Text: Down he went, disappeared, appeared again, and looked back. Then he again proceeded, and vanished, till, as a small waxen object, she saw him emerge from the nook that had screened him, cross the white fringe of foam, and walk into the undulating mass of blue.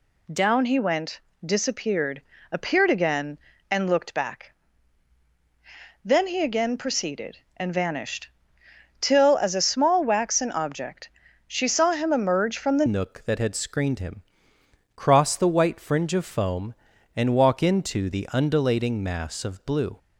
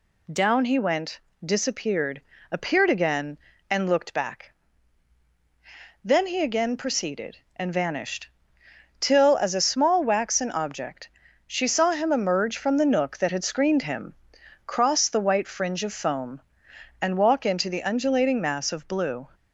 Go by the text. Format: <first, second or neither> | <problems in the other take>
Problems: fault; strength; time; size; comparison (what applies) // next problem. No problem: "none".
second | changes voice at "nook"; from 12.8 s on; 7.1 s long